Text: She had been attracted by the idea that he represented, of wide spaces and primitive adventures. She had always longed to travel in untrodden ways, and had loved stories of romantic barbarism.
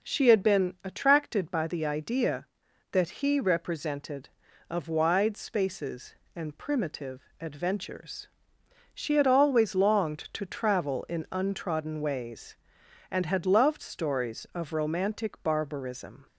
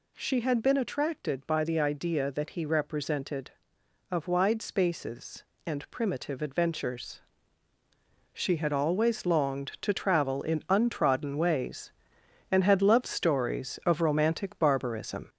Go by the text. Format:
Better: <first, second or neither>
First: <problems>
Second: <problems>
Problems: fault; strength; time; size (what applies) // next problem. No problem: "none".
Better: first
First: none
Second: gets louder; noticeable; throughout; 4 dB